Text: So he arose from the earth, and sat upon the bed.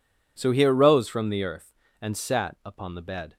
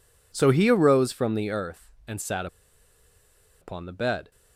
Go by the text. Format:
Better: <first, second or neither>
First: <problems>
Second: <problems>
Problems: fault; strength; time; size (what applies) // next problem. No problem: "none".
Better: first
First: none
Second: pauses between "sat" and "upon"; at 2.4 s; 1.1 s long